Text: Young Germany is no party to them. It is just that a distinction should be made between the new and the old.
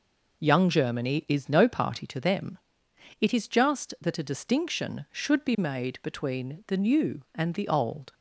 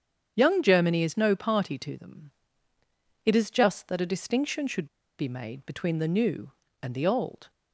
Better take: first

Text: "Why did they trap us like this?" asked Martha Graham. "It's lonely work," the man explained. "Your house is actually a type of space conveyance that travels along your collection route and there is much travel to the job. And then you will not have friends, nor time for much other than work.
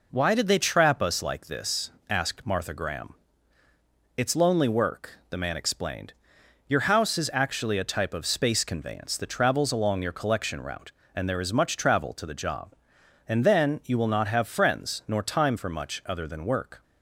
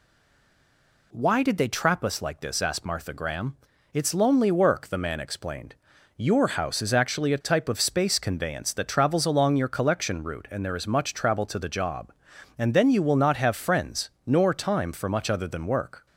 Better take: first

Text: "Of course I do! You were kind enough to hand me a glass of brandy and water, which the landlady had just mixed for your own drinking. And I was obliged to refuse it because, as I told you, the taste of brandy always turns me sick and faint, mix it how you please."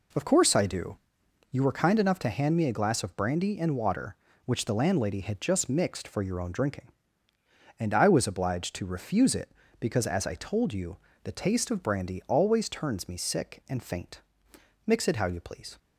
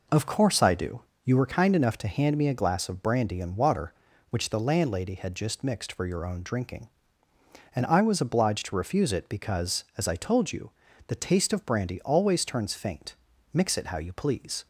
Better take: first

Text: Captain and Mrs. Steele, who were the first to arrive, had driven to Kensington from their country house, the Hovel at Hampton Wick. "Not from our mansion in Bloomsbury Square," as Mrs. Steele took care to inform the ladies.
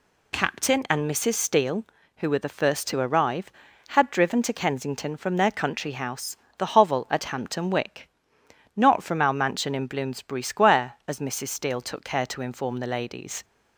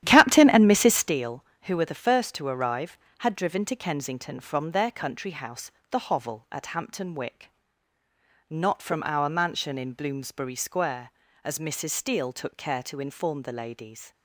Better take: first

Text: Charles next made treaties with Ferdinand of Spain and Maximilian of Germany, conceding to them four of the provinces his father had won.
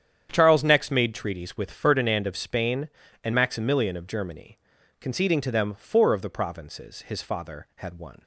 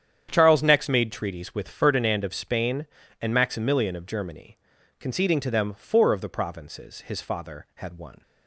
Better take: neither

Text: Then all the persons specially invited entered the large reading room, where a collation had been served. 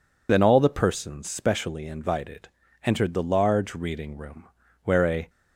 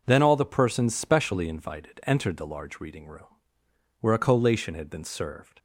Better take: second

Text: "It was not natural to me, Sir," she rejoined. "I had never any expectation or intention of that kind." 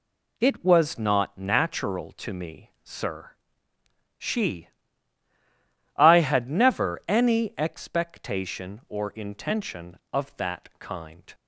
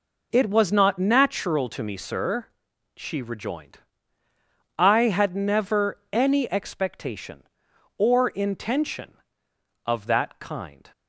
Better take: second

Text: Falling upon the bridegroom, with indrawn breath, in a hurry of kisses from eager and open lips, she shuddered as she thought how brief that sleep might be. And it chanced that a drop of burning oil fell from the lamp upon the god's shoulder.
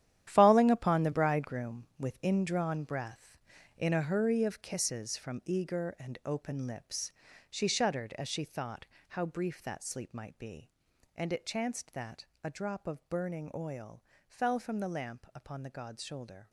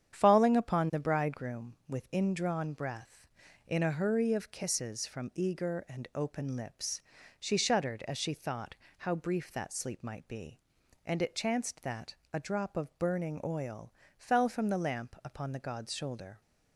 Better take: second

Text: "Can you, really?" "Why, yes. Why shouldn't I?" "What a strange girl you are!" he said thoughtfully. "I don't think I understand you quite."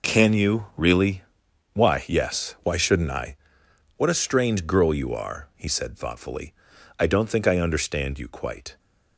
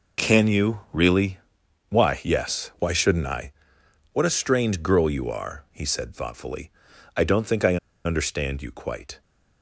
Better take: first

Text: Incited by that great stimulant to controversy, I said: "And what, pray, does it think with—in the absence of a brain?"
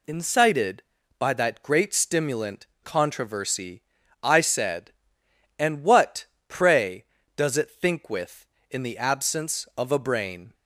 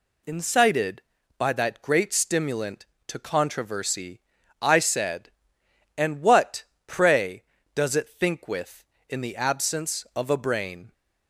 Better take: second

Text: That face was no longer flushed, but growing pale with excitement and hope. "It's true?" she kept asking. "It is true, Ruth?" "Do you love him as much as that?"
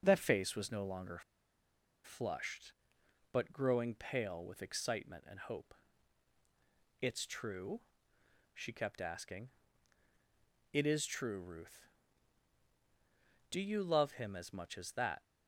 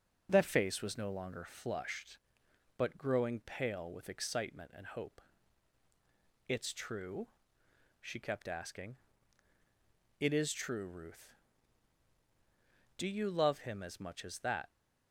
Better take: second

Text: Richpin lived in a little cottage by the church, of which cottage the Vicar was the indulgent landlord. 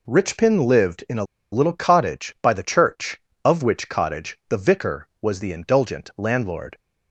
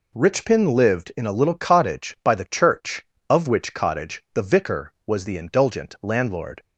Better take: second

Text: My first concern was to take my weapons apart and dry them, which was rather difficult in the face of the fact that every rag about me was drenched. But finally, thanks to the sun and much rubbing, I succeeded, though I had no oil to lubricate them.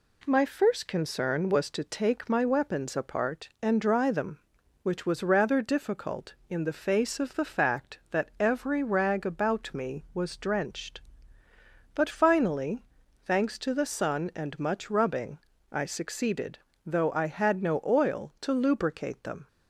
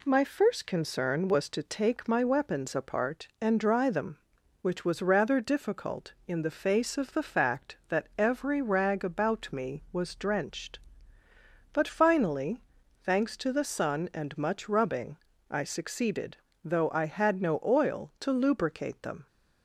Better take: neither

